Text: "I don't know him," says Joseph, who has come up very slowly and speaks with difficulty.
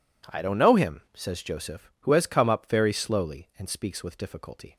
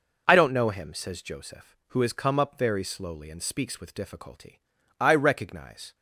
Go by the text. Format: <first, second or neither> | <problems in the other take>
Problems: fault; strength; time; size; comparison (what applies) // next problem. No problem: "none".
first | goes on to say "I recognize"; noticeable; from 4.9 s on; 0.96 s long